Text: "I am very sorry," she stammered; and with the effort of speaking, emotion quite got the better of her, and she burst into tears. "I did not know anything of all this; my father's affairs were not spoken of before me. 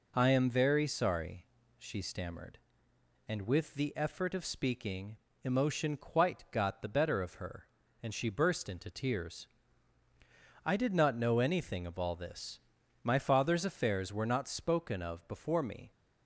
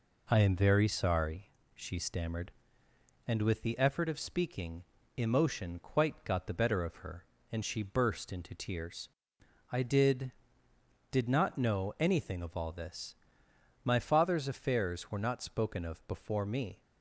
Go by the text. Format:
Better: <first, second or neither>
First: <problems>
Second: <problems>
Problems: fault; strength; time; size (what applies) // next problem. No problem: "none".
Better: first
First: none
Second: says "did" twice; at 11.1 s